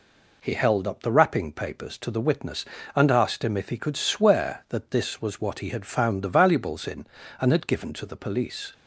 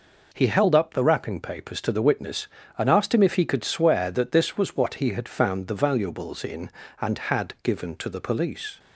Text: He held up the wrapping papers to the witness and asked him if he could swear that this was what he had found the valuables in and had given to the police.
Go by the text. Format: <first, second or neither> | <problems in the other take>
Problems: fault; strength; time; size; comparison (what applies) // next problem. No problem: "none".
neither | none